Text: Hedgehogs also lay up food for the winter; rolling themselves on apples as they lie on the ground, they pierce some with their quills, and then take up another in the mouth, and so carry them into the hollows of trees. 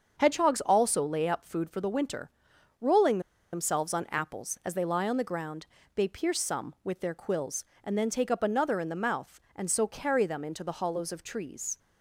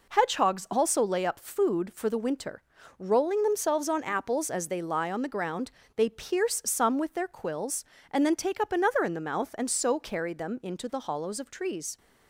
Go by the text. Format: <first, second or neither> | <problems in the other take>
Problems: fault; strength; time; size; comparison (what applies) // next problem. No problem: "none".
second | starts louder than the rest; until 1.2 s; 6.5 dB // pauses between "rolling" and "themselves"; slight; at 3.1 s; 0.33 s long